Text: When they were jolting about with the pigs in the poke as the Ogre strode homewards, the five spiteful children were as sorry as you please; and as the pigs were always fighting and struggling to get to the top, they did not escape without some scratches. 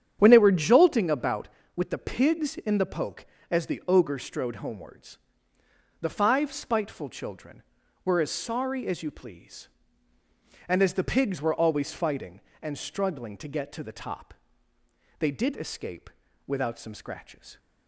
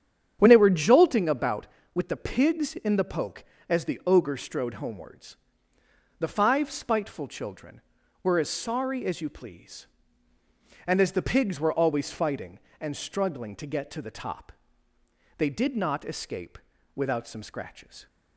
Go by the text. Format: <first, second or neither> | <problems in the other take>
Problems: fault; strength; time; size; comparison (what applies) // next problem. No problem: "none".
second | starts louder than the rest; strong; until 1.2 s; 9 dB; strong in the second // skips "not"; at 15.5 s // pauses between "escape" and "without"; at 16.0 s; 0.38 s long; also in the second